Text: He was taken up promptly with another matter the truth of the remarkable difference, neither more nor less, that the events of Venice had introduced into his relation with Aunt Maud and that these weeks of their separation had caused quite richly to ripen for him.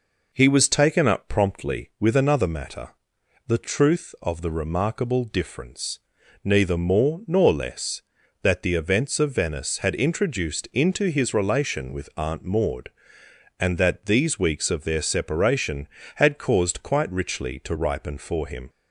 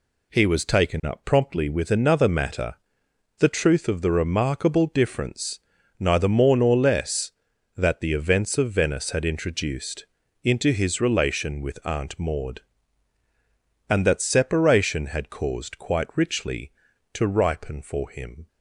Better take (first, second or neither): first